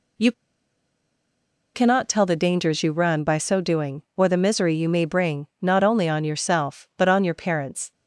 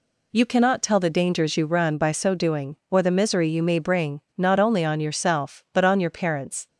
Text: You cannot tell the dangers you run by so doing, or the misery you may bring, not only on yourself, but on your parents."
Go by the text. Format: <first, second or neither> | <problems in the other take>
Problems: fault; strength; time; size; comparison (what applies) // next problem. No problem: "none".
second | pauses between "You" and "cannot"; strong; at 0.3 s; 1.4 s long